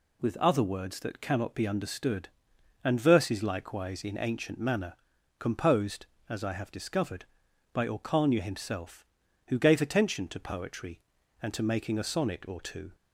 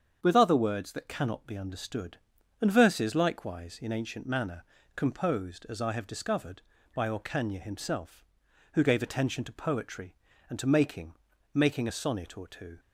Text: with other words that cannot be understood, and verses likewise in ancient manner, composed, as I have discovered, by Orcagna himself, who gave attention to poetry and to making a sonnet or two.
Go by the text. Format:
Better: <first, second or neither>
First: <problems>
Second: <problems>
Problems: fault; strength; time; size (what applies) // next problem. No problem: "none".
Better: first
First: none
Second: starts louder than the rest; strong; until 1.2 s; 7.5 dB // says "making" twice; at 11.5 s